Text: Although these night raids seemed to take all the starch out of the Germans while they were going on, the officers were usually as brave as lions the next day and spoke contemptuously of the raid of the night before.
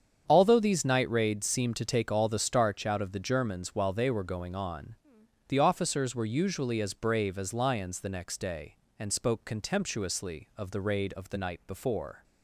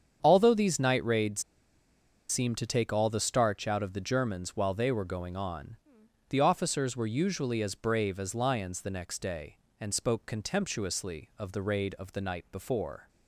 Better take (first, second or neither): first